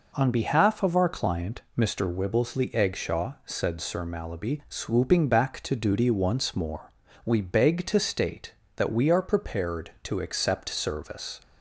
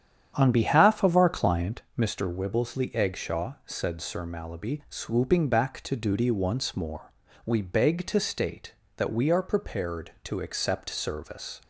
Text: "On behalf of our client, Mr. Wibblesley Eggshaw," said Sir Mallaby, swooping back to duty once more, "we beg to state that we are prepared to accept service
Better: first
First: none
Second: starts louder than the rest; strong; until 1.8 s; 9 dB

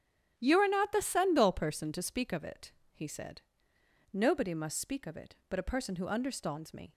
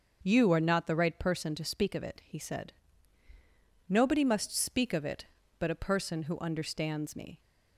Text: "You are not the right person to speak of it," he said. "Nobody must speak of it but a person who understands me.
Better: second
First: starts louder than the rest; strong; until 1.3 s; 9 dB // says "sendal" for "right"; at 1.0 s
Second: starts louder than the rest; until 1.2 s; 6.5 dB

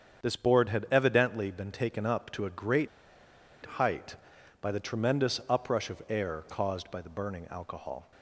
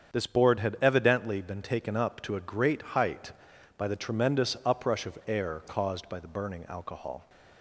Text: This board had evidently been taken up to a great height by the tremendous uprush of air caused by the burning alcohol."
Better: second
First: starts louder than the rest; strong; until 1.2 s; 7.5 dB // pauses between "great" and "height"; noticeable; at 2.8 s; 0.76 s long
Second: starts louder than the rest; strong; until 1.1 s; 7.5 dB

